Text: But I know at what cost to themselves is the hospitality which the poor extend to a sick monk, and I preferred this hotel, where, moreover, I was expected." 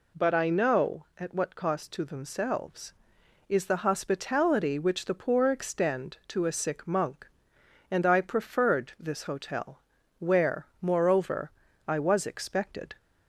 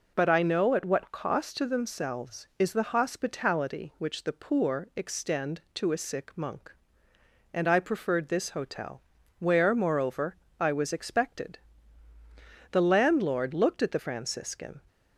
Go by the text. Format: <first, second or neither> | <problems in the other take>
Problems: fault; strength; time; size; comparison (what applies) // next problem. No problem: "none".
first | goes on to say "The landlord looked at the Franciscan"; strong; from 12.7 s on; 2.1 s long